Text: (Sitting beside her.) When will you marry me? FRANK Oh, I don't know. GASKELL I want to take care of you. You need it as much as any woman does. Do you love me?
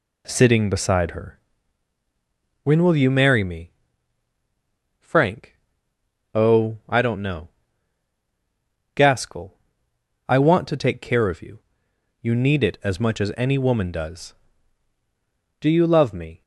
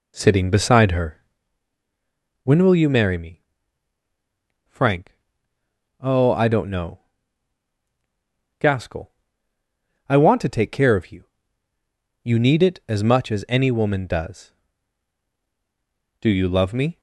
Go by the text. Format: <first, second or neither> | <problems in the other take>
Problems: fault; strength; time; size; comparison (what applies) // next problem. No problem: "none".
first | starts louder than the rest; slight; until 1.5 s; 3 dB // pauses between "FRANK" and "Oh"; noticeable; at 5.0 s; 0.90 s long; noticeable in the first // pauses between "GASKELL" and "I"; noticeable; at 9.0 s; 0.98 s long; noticeable in the first